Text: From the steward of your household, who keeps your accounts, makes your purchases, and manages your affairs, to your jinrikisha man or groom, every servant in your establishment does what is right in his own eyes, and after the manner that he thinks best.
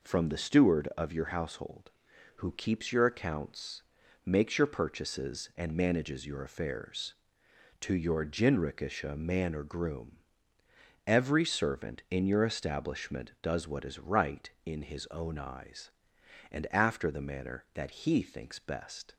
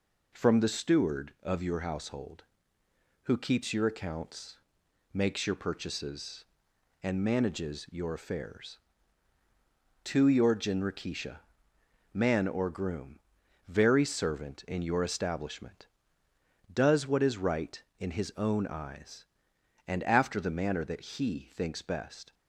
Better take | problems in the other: first | pauses between "jinrikisha" and "man"; noticeable; at 11.3 s; 0.74 s long // says "very" for "every"; at 13.6 s

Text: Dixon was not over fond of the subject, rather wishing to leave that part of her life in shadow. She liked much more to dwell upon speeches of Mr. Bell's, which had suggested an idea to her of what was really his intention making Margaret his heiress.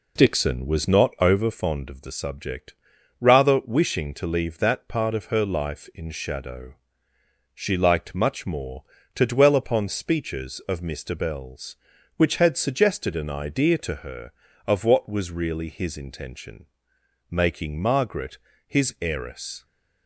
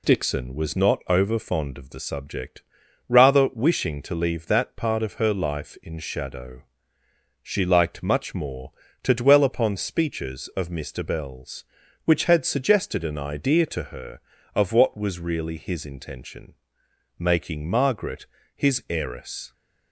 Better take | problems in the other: second | starts louder than the rest; slight; until 1.6 s; 3 dB // pauses between "intention" and "making"; noticeable; at 16.6 s; 0.64 s long; noticeable in the second // pauses between "Margaret" and "his"; slight; at 18.3 s; 0.30 s long; slight in the second

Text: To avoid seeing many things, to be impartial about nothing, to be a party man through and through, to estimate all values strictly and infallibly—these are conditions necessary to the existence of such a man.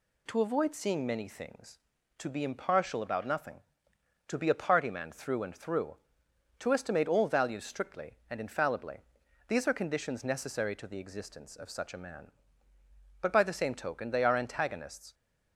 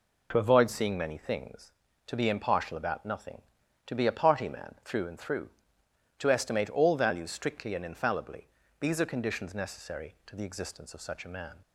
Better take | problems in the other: second | goes on to say "But by the same token they are antagonists"; strong; from 13.2 s on; 1.9 s long

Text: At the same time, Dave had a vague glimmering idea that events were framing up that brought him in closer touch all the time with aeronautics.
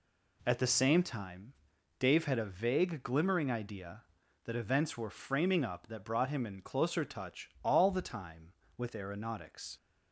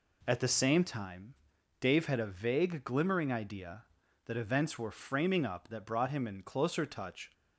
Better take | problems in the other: first | stops before "all the time with aeronautics"; at 7.3 s

